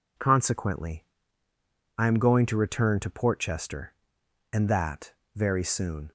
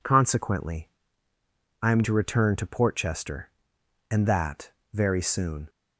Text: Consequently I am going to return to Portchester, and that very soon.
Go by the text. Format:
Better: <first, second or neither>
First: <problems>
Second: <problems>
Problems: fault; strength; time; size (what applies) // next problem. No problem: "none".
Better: first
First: pauses between "Consequently" and "I"; noticeable; at 1.0 s; 0.94 s long // pauses between "that" and "very"; slight; at 5.1 s; 0.22 s long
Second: pauses between "Consequently" and "I"; noticeable; at 0.8 s; 0.94 s long // skips "going"; at 2.0 s // pauses between "that" and "very"; slight; at 4.7 s; 0.22 s long